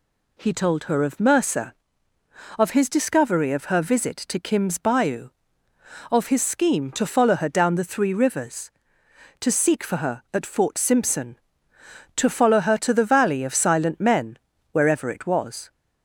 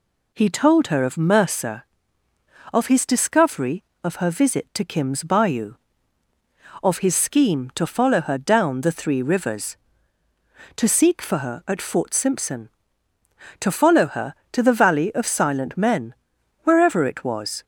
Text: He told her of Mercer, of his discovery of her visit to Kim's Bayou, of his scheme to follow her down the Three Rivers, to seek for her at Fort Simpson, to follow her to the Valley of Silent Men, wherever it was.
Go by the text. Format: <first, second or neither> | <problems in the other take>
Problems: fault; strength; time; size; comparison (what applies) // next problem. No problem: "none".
neither | none